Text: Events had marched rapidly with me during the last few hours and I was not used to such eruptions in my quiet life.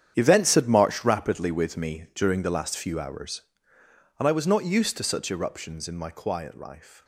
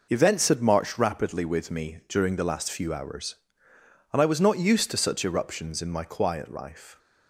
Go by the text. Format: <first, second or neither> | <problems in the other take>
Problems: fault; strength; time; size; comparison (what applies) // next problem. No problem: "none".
second | gets quieter; strong; throughout; 13.5 dB